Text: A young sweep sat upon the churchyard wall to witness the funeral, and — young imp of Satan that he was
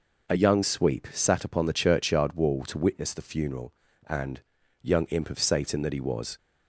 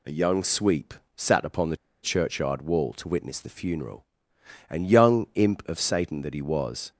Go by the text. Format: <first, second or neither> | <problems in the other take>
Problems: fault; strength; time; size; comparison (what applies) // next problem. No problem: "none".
first | pauses between "sweep" and "sat"; slight; at 0.9 s; 0.22 s long // pauses between "the" and "churchyard"; slight; at 1.7 s; 0.25 s long